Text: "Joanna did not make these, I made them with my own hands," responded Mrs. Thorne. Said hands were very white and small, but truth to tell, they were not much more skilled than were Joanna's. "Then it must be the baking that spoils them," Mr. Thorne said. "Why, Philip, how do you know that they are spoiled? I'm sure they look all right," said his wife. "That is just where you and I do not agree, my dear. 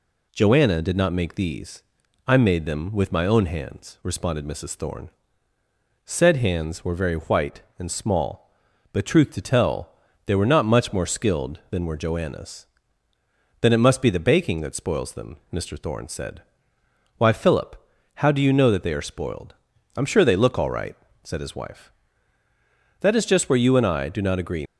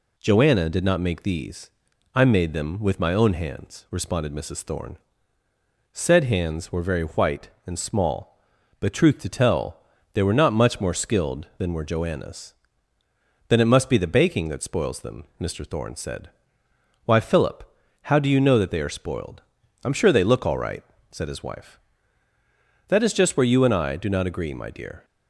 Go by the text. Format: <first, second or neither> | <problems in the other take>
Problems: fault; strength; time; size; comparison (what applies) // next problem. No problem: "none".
second | stops before "my dear"; at 24.6 s